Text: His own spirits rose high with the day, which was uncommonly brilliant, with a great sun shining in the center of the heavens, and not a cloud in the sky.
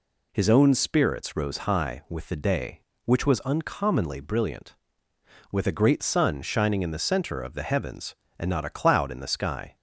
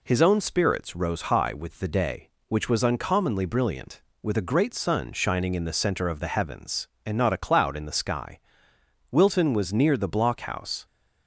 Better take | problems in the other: first | goes on to say "Wilton was near the blockhouse"; strong; from 9.1 s on; 1.7 s long

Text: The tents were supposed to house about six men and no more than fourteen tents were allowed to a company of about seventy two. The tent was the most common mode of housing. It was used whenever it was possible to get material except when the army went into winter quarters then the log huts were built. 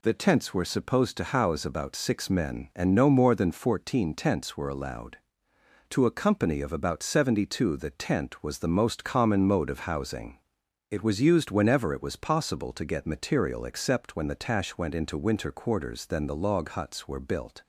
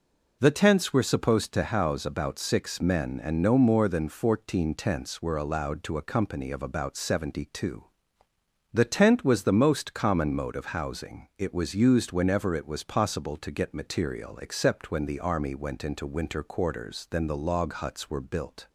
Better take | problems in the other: second | says "tash" for "army"; at 14.3 s

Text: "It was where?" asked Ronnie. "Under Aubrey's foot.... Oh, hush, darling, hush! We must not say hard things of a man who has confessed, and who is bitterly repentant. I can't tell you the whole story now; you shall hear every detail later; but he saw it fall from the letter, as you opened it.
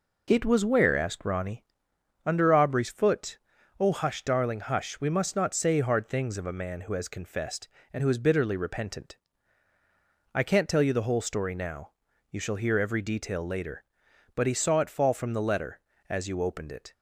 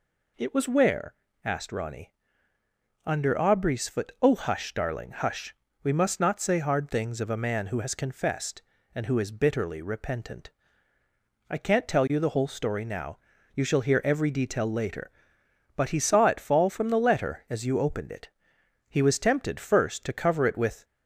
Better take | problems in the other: first | goes on to say "He was tempted first to cover it with"; strong; from 18.8 s on; 1.9 s long

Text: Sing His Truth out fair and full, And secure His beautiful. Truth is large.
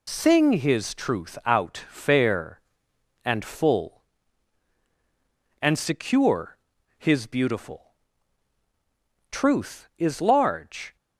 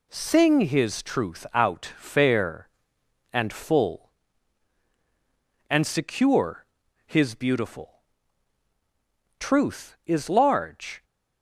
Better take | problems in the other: second | loses the start of "Sing"; at 0.0 s; 60 ms // pauses between "secure" and "His"; at 6.5 s; 0.40 s long; also in the second

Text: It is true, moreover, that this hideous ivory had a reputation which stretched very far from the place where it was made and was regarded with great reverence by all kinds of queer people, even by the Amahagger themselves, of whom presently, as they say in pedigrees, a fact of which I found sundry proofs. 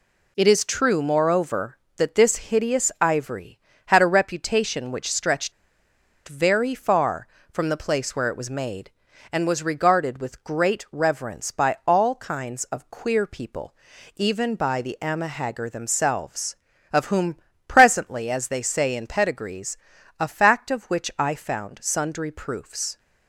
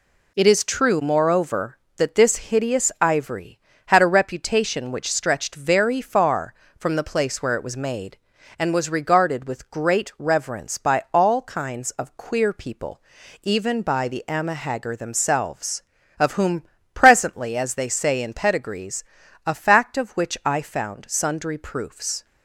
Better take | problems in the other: second | pauses between "stretched" and "very"; noticeable; at 5.5 s; 0.76 s long // pauses between "whom" and "presently"; slight; at 17.3 s; 0.30 s long; slight in the second

